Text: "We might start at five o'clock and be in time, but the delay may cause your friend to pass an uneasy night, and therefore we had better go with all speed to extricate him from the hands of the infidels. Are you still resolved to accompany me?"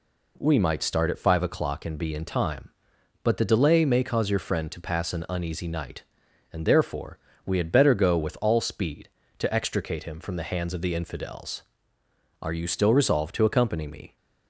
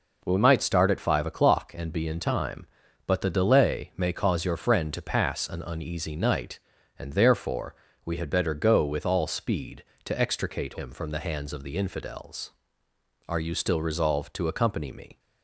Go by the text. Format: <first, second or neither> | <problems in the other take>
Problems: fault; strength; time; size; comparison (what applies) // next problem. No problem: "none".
neither | pauses between "therefore" and "we"; slight; the same in both